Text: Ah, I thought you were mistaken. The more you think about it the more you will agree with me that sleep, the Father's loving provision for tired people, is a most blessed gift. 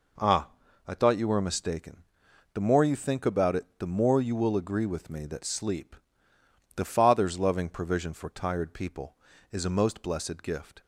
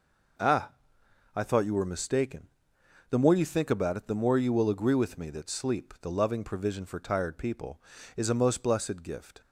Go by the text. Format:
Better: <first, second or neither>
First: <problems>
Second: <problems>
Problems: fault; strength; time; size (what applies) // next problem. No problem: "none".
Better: first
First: none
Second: skips "Father's"; at 6.1 s